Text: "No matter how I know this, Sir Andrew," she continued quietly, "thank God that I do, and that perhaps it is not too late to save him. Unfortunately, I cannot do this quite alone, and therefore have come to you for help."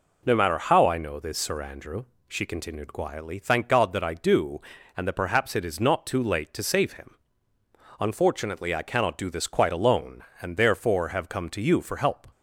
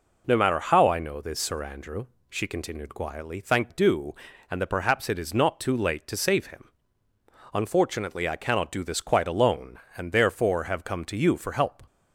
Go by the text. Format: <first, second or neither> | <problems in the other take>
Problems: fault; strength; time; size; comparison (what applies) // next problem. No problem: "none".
first | skips "God that I"; at 3.6 s